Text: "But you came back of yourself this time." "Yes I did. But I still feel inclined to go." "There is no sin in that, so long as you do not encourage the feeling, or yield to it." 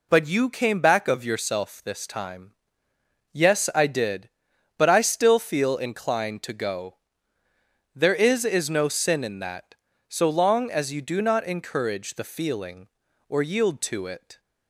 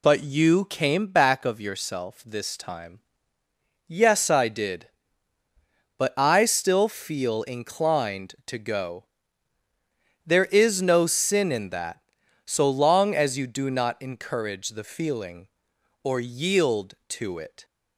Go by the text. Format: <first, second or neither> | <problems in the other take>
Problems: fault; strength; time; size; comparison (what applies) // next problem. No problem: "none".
second | says "is" twice; at 8.4 s